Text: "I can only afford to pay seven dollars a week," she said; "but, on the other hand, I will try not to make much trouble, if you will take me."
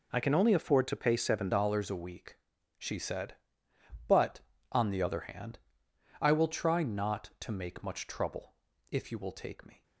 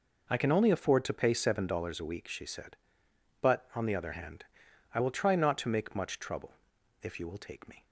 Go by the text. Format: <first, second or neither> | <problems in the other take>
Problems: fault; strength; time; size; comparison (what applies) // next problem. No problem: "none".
second | changes voice at "dollars"; from 1.5 s on; 8.3 s long